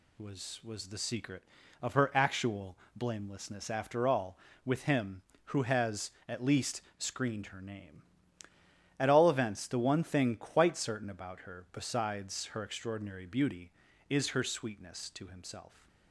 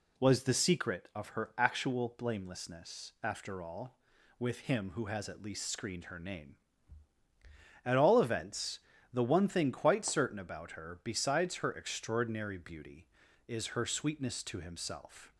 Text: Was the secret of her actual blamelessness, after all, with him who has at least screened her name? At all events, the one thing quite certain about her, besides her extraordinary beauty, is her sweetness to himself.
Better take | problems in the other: second | says "Was" twice; at 0.6 s // pauses between "actual" and "blamelessness"; slight; at 2.7 s; 0.18 s long // pauses between "least" and "screened"; slight; at 6.8 s; 0.16 s long

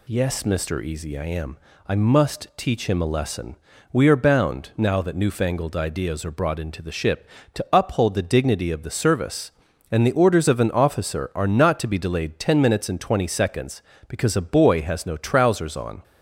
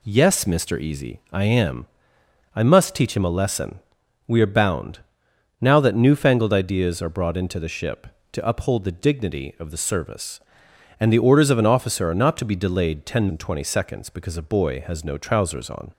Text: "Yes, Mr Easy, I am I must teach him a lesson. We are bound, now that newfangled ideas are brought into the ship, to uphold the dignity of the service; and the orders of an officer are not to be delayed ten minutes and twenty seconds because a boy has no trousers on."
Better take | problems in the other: first | pauses between "am" and "I"; noticeable; at 1.8 s; 0.70 s long; slight in the first // skips "minutes"; at 13.2 s

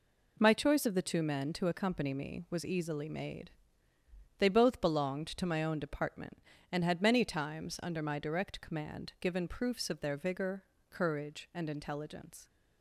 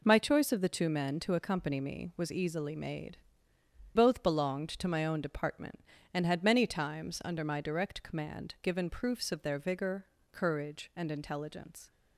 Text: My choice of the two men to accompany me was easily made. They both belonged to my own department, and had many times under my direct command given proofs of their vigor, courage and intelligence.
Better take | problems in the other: first | skips "They"; at 3.5 s

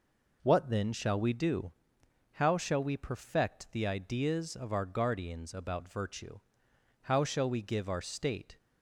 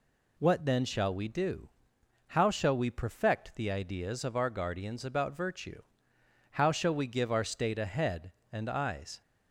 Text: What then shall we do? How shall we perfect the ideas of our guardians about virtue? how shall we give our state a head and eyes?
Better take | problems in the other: second | stops before "a head and eyes"; at 8.5 s

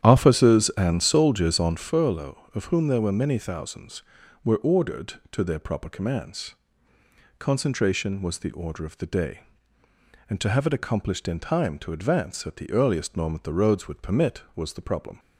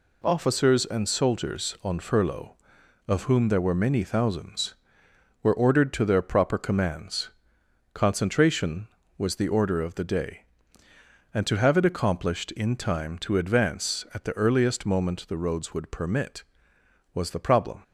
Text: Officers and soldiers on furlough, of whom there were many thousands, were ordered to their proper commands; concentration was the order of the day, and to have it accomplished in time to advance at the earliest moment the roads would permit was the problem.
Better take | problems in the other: second | starts louder than the rest; strong; until 1.9 s; 10.5 dB

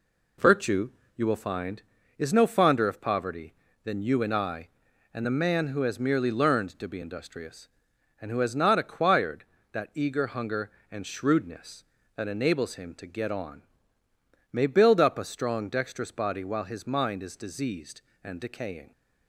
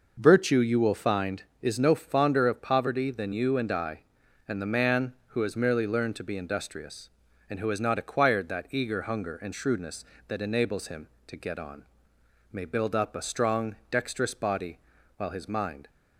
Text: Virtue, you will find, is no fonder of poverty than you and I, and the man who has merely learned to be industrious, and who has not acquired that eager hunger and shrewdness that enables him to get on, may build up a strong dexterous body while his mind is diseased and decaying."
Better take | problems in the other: first | pauses between "strong" and "dexterous"; slight; at 13.7 s; 0.16 s long // pauses between "body" and "while"; at 14.7 s; 0.38 s long // stops before "is diseased and decaying"; at 15.8 s

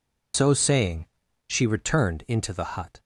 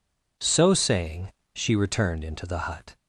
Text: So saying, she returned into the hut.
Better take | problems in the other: second | loses the start of "So"; at 0.3 s; 85 ms

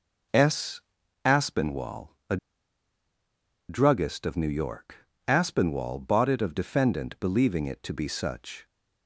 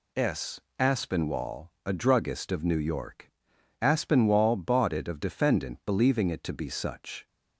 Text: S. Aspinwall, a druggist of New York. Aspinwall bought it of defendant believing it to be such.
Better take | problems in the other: second | pauses between "a" and "druggist"; strong; at 2.3 s; 1.3 s long

